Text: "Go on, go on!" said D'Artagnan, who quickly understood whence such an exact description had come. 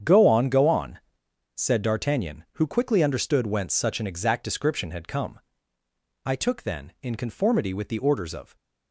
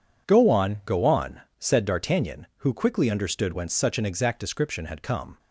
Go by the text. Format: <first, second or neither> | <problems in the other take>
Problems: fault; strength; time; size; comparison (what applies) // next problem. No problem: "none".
second | starts louder than the rest; strong; until 1.5 s; 8 dB // goes on to say "I took then in conformity with the orders of"; strong; from 6.2 s on; 2.3 s long